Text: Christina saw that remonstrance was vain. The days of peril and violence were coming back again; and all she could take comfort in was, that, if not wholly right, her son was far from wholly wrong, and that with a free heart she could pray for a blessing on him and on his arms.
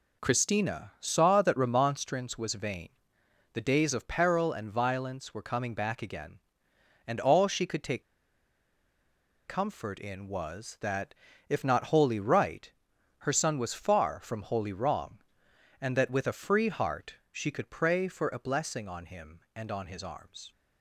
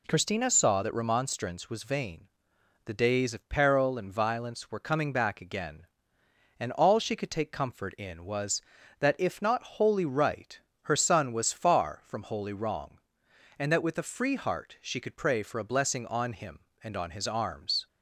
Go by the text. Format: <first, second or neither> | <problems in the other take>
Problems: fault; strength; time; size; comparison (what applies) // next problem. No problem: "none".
second | pauses between "take" and "comfort"; strong; at 8.0 s; 1.4 s long // pauses between "heart" and "she"; slight; at 17.1 s; 0.16 s long